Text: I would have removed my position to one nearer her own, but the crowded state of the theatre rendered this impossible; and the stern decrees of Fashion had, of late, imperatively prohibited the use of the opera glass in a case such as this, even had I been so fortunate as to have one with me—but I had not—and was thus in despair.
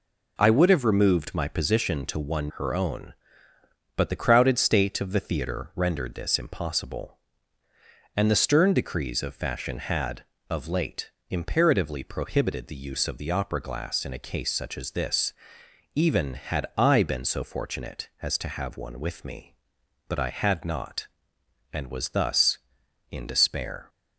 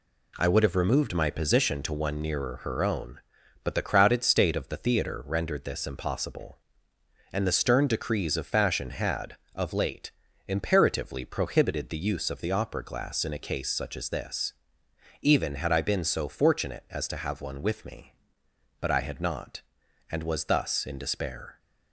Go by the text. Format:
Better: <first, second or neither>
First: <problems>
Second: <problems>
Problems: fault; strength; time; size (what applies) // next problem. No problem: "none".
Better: second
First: skips "nearer"; at 2.5 s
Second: none